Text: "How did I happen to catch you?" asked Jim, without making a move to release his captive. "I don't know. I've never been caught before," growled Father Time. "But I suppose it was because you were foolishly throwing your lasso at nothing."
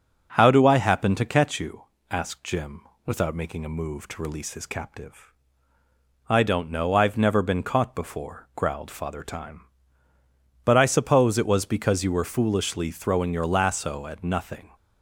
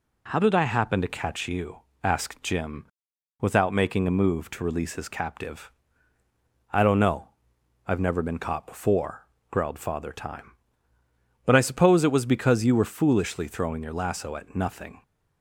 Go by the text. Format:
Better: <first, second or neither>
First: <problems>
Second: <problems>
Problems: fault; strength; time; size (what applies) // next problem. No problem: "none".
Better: second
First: starts louder than the rest; until 1.3 s; 6.5 dB // says "do" for "did"; at 0.4 s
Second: none